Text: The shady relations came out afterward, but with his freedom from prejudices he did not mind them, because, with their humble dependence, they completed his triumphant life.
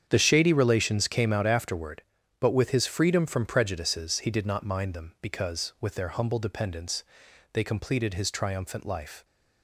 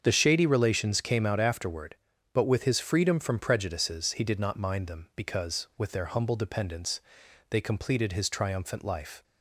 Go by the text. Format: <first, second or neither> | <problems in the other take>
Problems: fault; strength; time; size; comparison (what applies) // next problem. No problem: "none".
second | gets quieter; strong; throughout; 12 dB // starts louder than the rest; strong; until 1.0 s; 8 dB; also in the second